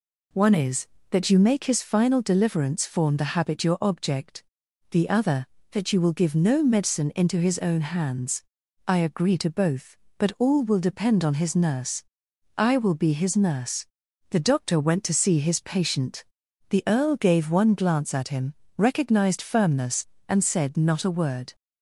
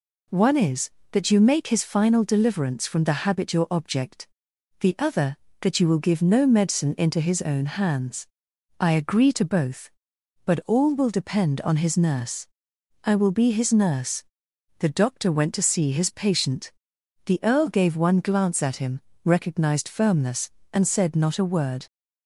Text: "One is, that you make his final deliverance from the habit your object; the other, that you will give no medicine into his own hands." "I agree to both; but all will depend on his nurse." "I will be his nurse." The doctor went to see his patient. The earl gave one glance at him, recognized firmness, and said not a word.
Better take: second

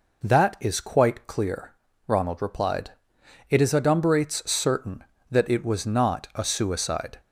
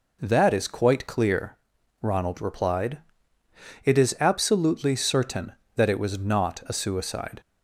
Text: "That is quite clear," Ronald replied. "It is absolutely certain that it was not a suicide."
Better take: second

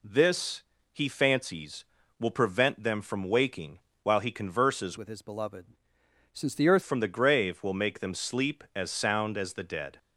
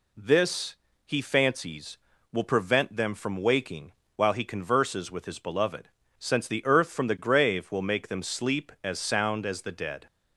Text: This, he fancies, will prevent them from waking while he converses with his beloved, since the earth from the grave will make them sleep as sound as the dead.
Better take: second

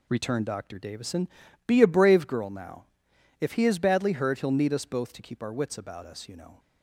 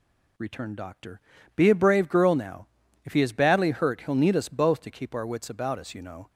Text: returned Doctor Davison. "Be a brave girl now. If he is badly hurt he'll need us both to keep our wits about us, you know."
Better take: first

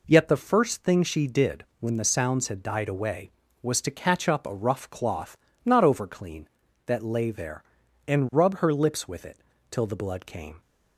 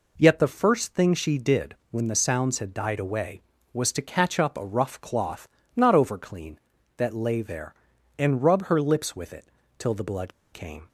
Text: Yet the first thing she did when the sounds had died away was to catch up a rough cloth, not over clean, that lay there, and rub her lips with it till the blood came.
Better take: first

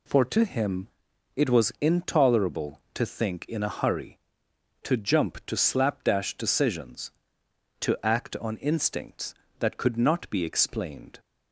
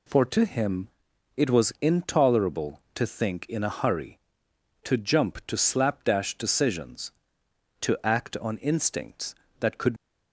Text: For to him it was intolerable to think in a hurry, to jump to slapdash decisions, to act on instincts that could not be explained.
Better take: first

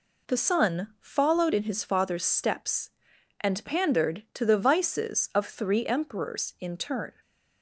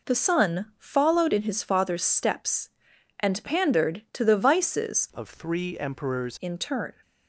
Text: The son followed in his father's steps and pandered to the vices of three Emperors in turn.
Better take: first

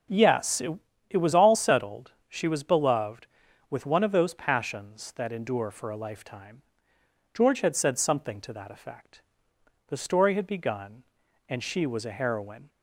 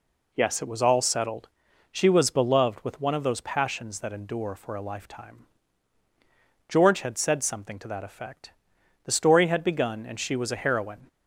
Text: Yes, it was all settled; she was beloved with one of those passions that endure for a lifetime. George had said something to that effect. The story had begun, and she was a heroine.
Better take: second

